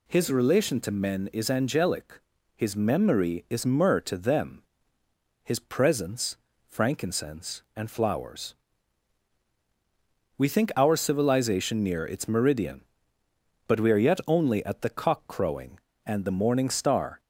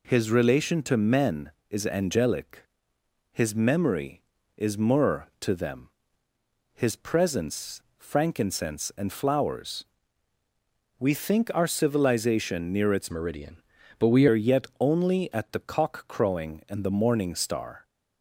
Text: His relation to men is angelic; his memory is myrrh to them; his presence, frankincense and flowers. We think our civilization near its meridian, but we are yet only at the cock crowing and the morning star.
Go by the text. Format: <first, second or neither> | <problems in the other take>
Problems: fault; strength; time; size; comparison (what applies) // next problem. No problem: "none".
first | changes voice from "meridian" to "we"; from 13.0 to 14.2 s; 1.2 s long